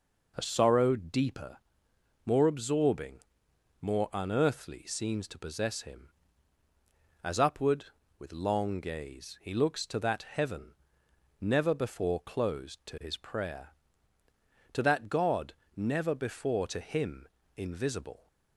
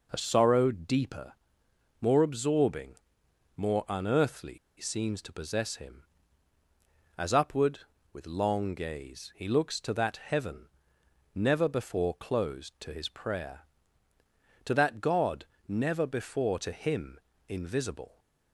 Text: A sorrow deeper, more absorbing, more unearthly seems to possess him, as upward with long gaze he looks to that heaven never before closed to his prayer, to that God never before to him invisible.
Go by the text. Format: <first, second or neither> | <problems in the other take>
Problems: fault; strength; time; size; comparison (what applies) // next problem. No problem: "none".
first | pauses between "unearthly" and "seems"; slight; at 4.5 s; 0.20 s long // pauses between "heaven" and "never"; noticeable; at 10.6 s; 0.66 s long; noticeable in the first // pauses between "God" and "never"; slight; at 15.4 s; 0.22 s long; slight in the first // pauses between "him" and "invisible"; slight; at 17.1 s; 0.28 s long; slight in the first